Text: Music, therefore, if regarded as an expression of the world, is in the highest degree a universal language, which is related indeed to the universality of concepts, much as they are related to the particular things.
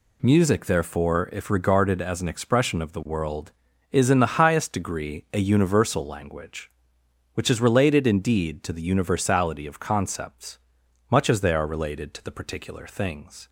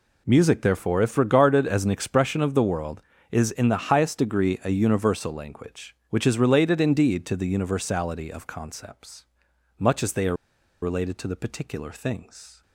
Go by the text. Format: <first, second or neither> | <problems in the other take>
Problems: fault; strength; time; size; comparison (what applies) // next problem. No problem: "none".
first | pauses between "are" and "related"; noticeable; at 10.3 s; 0.46 s long